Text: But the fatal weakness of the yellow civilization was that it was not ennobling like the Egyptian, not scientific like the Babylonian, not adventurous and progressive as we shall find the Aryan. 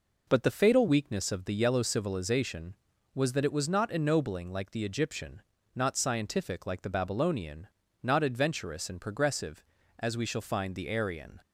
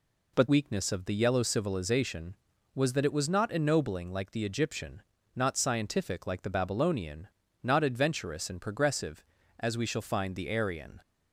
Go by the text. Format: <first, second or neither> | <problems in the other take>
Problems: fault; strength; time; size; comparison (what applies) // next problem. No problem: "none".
first | skips "the fatal"; at 0.4 s